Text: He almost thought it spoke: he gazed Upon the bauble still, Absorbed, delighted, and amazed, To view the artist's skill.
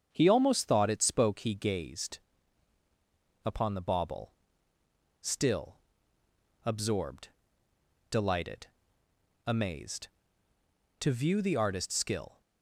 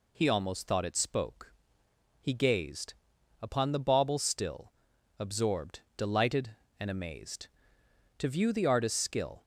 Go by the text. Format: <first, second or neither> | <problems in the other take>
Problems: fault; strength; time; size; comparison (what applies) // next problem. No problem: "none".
second | starts louder than the rest; strong; until 1.1 s; 7 dB // pauses between "gazed" and "Upon"; strong; at 2.1 s; 1.2 s long; noticeable in the second // pauses between "bauble" and "still"; noticeable; at 4.3 s; 0.88 s long // skips "and"; at 9.0 s